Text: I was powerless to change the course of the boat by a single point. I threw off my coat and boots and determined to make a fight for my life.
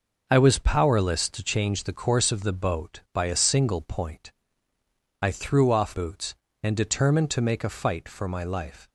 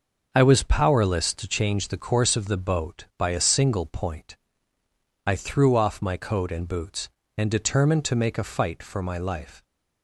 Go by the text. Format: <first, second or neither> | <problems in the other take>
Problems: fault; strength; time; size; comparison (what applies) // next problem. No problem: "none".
second | skips "my coat and"; at 5.9 s